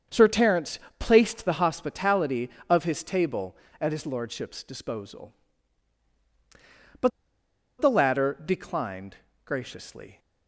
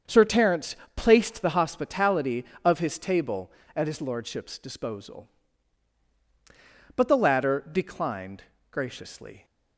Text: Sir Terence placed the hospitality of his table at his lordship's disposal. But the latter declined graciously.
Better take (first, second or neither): second